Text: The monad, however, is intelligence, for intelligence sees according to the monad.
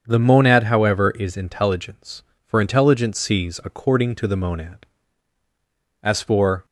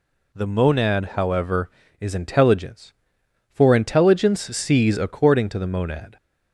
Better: second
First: starts louder than the rest; until 1.0 s; 7 dB // goes on to say "As for"; noticeable; from 6.0 s on; 0.62 s long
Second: none

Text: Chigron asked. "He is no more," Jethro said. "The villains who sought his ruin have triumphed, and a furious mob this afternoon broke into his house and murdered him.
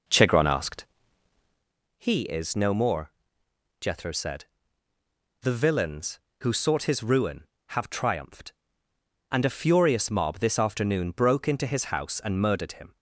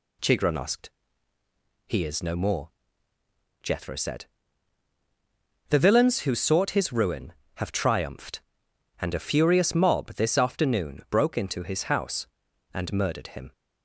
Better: second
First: starts louder than the rest; noticeable; until 1.8 s; 5 dB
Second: none

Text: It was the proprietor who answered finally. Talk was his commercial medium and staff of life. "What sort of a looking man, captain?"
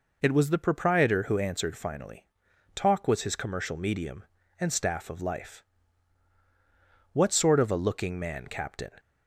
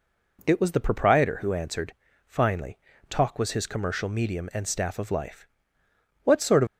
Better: first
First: none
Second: pauses between "answered" and "finally"; slight; at 1.9 s; 0.34 s long // stops before "a looking man captain"; at 6.6 s

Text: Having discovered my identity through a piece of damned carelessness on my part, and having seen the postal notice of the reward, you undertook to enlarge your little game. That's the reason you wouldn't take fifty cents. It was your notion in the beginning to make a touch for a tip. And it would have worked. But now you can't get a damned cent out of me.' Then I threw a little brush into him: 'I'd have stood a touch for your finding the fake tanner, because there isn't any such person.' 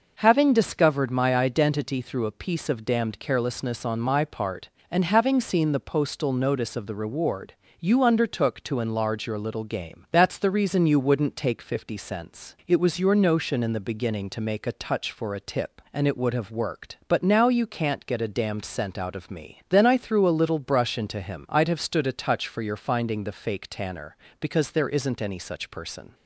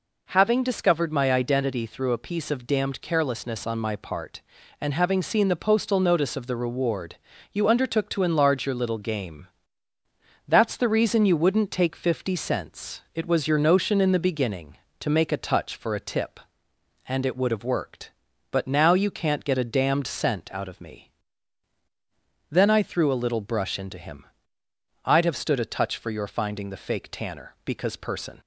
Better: first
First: none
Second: skips "there isn't any such"; at 27.9 s

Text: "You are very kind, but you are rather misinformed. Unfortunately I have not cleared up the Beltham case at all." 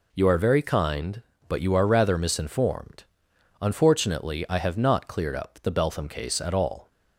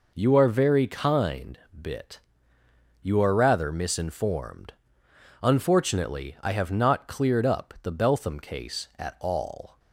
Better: first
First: none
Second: says "bit" for "but"; at 1.7 s

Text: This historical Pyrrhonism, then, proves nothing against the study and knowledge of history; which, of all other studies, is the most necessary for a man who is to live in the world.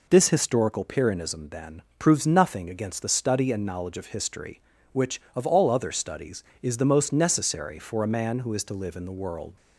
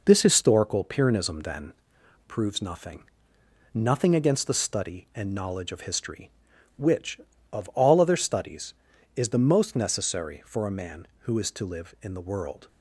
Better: first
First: none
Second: says "nothing" twice; at 3.7 s

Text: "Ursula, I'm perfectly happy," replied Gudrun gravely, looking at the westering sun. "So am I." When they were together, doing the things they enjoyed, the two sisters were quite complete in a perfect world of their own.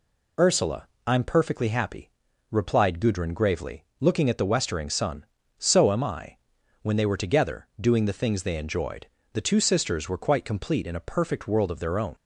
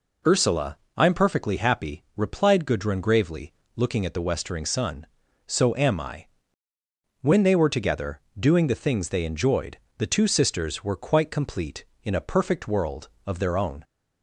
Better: neither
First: none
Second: none

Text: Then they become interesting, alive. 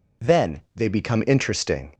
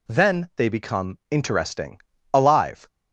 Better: second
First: stops before "alive"; at 1.9 s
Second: none

